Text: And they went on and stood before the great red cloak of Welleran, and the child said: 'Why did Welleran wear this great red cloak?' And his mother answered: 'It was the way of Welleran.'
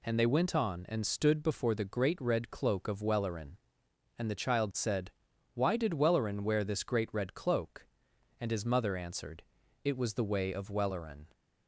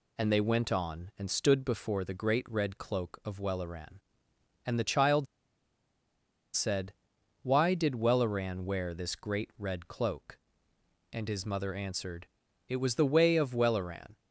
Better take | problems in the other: first | pauses between "child" and "said"; strong; at 5.2 s; 1.2 s long

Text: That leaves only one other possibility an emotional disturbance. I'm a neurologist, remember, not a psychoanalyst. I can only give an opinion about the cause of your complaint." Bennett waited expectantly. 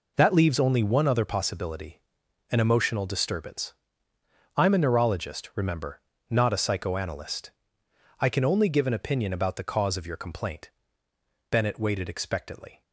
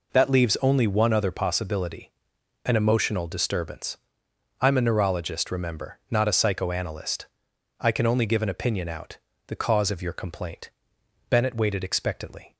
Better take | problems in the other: first | pauses between "possibility" and "an"; noticeable; at 2.0 s; 0.56 s long; noticeable in the first // says "out" for "about"; at 8.8 s

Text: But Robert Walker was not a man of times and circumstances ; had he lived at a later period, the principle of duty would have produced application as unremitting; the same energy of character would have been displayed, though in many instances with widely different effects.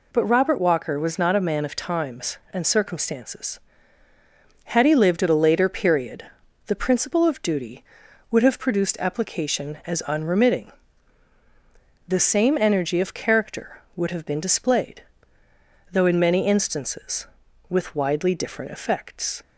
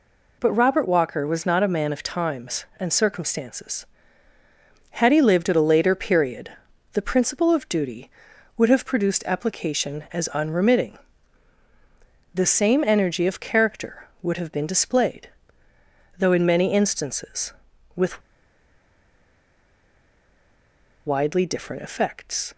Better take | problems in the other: first | pauses between "with" and "widely"; strong; at 18.2 s; 2.8 s long

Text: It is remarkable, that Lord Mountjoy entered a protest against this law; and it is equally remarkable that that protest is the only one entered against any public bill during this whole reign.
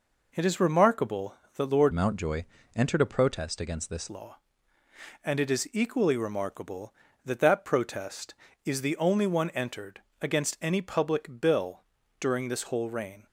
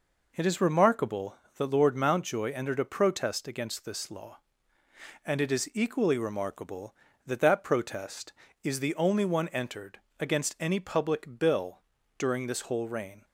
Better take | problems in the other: second | changes voice from "Mountjoy" to "this"; from 1.9 to 4.0 s; 2.1 s long // pauses between "Mountjoy" and "entered"; slight; at 2.4 s; 0.30 s long // pauses between "entered" and "against"; slight; at 9.9 s; 0.22 s long; slight in the second // pauses between "bill" and "during"; slight; at 11.8 s; 0.36 s long; slight in the second

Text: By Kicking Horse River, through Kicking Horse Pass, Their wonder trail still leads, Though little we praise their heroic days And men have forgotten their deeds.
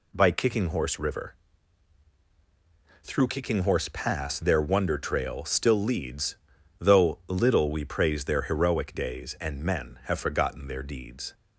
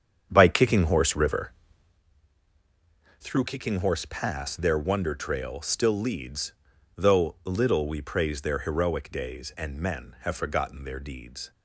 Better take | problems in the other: first | starts louder than the rest; strong; until 2.0 s; 8 dB

